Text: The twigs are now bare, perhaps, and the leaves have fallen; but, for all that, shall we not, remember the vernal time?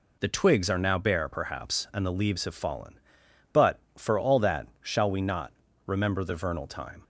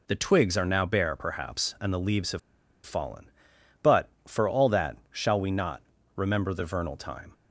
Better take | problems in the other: first | pauses between "have" and "fallen"; at 2.3 s; 0.45 s long

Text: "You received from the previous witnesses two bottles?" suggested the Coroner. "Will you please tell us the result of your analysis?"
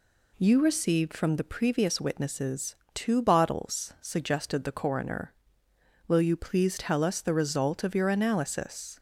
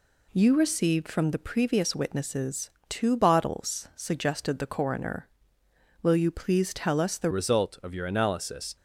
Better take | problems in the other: first | pauses between "witnesses" and "two"; slight; at 2.6 s; 0.18 s long; slight in the first // changes voice at "result"; from 7.3 s on; 1.4 s long

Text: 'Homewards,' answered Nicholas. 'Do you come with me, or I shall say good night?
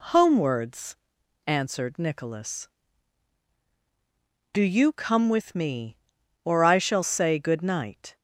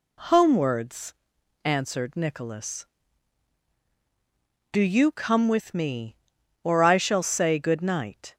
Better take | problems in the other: neither | none

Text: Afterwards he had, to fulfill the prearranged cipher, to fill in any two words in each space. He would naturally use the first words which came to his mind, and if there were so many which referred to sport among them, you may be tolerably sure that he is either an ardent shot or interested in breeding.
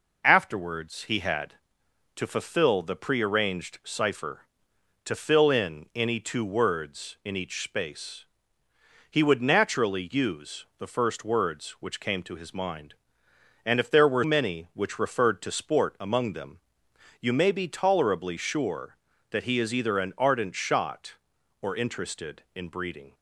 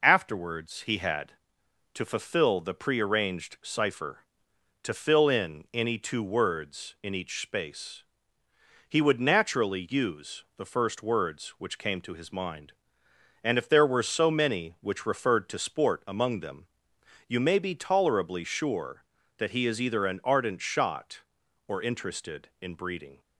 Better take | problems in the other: second | skips "so"; at 14.2 s

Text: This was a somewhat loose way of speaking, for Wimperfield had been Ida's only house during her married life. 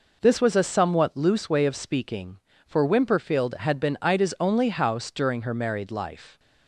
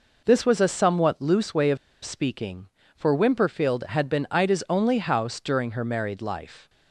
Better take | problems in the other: first | pauses between "of" and "speaking"; slight; at 1.7 s; 0.25 s long

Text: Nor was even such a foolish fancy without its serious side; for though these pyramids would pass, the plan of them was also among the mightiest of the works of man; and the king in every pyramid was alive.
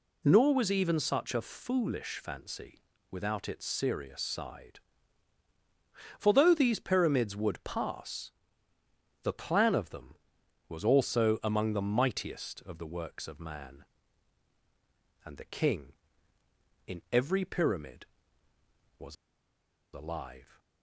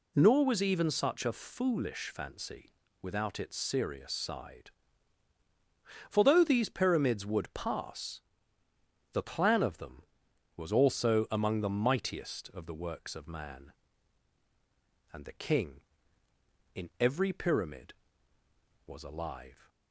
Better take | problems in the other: second | pauses between "fancy" and "without"; slight; at 2.7 s; 0.32 s long; slight in the second // pauses between "was" and "alive"; noticeable; at 19.1 s; 0.79 s long

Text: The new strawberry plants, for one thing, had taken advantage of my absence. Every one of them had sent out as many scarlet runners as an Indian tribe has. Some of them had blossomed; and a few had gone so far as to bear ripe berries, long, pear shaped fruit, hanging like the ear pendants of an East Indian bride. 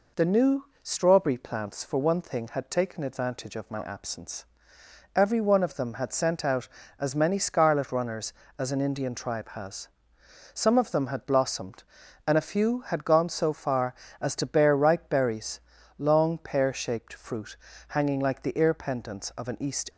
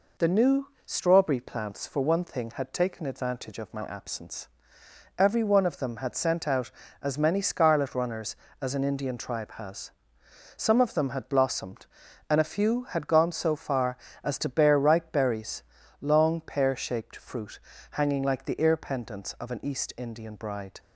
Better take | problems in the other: second | pauses between "new" and "strawberry"; slight; at 0.6 s; 0.16 s long; slight in the second // stops before "Indian bride"; at 19.8 s

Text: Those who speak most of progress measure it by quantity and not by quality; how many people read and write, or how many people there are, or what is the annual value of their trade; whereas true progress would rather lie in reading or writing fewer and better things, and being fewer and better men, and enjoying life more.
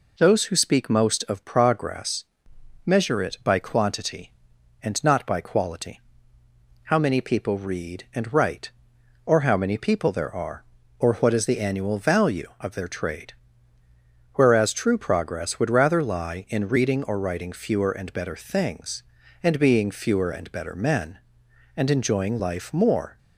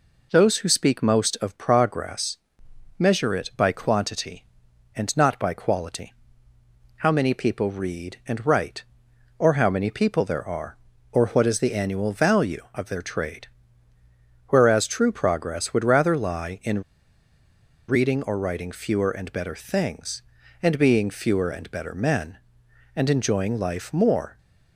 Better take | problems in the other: first | pauses between "progress" and "measure"; noticeable; at 2.3 s; 0.60 s long; noticeable in the first // pauses between "in" and "reading"; at 16.8 s; 1.0 s long

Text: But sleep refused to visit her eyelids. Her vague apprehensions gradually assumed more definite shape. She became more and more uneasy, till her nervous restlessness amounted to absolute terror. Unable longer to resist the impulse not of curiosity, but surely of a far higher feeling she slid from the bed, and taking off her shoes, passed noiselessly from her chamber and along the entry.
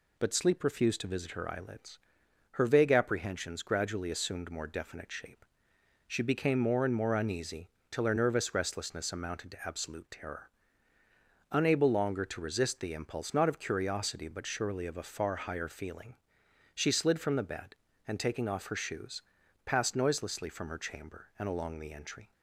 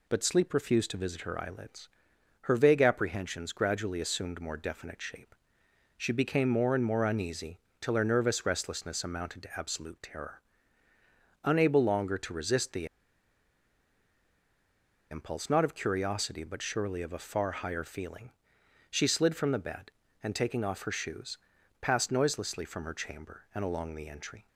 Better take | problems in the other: first | pauses between "the" and "impulse"; strong; at 12.8 s; 2.2 s long // pauses between "feeling" and "she"; noticeable; at 18.3 s; 0.60 s long; noticeable in the first

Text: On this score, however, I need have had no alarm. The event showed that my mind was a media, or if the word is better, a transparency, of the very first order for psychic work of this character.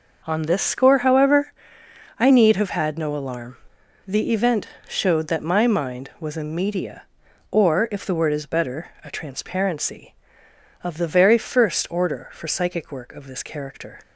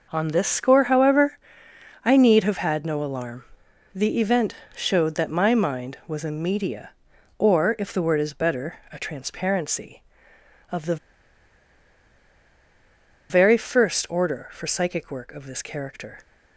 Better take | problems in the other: first | pauses between "event" and "showed"; slight; at 4.5 s; 0.20 s long; slight in the first // pauses between "the" and "very"; strong; at 10.9 s; 2.3 s long

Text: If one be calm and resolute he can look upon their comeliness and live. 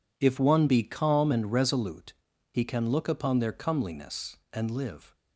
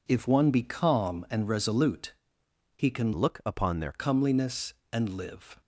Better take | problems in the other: first | pauses between "resolute" and "he"; noticeable; at 2.1 s; 0.64 s long; also in the first // changes voice from "look" to "their"; from 3.1 to 3.9 s; 0.8 s long

